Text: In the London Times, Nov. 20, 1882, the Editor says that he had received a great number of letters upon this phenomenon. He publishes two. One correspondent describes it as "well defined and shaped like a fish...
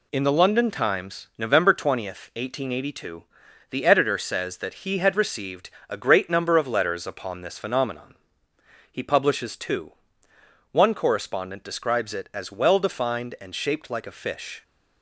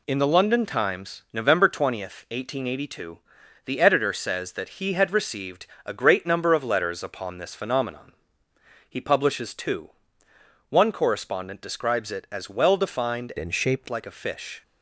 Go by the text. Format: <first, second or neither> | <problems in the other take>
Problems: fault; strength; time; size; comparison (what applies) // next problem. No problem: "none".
first | pauses between "received" and "a"; slight; at 5.6 s; 0.20 s long; slight in the first // changes voice from "and" to "shaped"; from 13.3 to 13.8 s; 0.5 s long